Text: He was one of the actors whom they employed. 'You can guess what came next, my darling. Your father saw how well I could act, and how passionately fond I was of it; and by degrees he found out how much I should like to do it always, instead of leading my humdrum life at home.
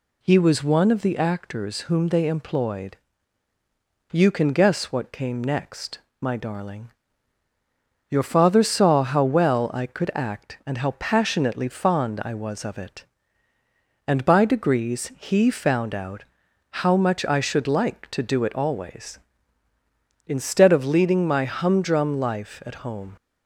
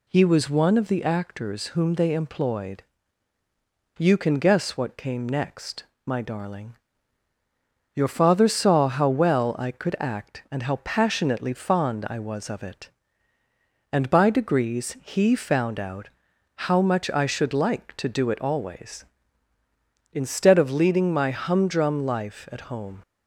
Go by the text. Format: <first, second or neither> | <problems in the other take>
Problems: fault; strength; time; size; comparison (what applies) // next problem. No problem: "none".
neither | pauses between "out" and "how"; noticeable; the same in both